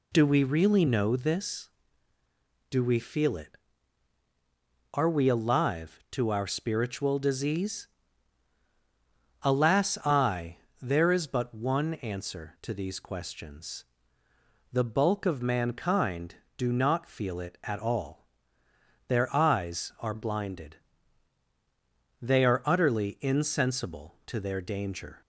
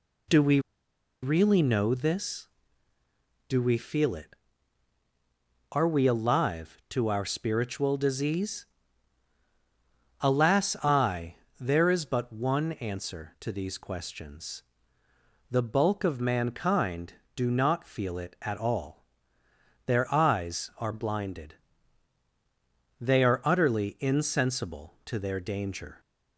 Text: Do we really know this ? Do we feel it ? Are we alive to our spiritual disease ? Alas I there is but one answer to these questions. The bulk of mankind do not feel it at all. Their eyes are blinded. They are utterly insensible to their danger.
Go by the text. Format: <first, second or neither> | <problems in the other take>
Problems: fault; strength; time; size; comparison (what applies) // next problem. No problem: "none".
first | pauses between "we" and "really"; noticeable; at 0.5 s; 0.63 s long // pauses between "I" and "there"; slight; at 11.3 s; 0.24 s long; slight in the first